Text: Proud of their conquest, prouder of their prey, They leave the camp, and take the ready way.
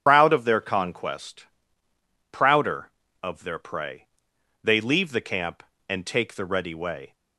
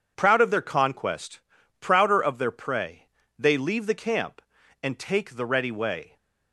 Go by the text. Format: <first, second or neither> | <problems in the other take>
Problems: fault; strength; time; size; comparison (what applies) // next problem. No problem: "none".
second | loses the start of "Proud"; at 0.0 s; 85 ms // starts louder than the rest; strong; until 1.0 s; 9 dB